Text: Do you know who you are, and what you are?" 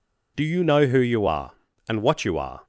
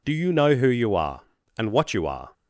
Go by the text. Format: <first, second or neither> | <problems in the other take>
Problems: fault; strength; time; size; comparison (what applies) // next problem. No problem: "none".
neither | none